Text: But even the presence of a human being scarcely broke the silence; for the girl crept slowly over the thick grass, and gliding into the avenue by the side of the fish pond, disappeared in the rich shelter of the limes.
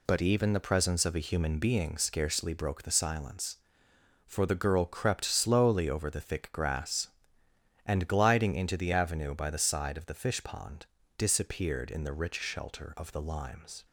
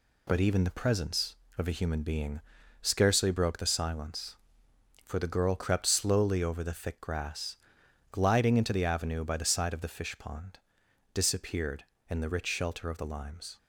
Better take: first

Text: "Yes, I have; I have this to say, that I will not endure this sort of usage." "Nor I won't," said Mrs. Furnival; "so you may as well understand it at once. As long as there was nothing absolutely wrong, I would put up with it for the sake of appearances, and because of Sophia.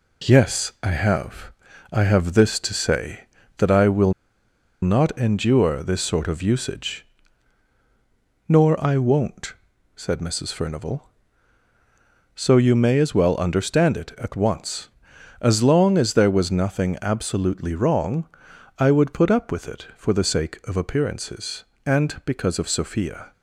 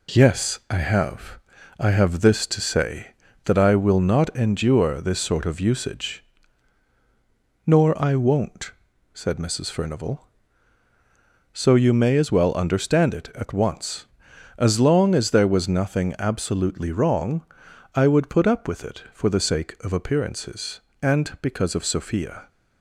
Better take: second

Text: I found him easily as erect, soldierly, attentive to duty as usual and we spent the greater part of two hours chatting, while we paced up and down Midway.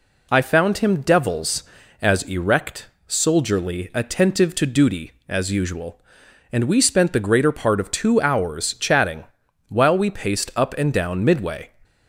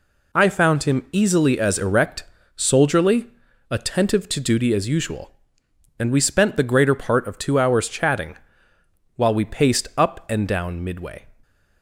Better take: second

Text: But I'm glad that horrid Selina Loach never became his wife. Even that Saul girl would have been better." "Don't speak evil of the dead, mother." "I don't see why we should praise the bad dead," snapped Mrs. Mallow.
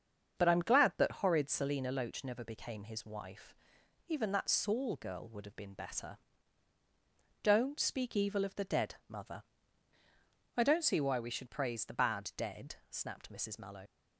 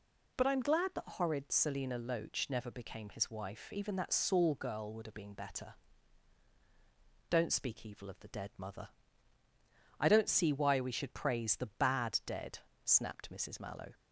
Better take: second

